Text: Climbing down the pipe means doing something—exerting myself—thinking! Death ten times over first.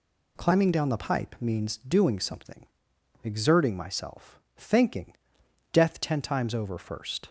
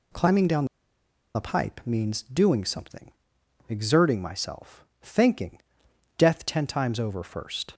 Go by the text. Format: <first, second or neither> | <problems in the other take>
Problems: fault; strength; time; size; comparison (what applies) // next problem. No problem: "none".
first | pauses between "down" and "the"; noticeable; at 0.6 s; 0.68 s long